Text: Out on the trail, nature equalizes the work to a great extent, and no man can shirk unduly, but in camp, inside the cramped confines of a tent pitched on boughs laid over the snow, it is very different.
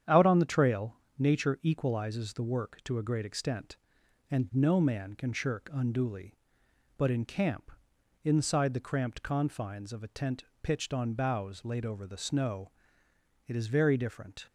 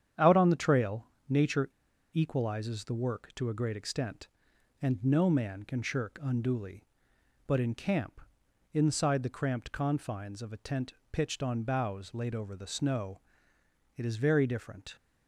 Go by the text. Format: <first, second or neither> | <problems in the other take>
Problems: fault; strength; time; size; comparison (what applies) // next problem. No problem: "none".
first | starts louder than the rest; strong; until 1.3 s; 9 dB; strong in the first // pauses between "nature" and "equalizes"; at 1.6 s; 0.44 s long // pauses between "tent" and "pitched"; slight; at 10.9 s; 0.18 s long; slight in the first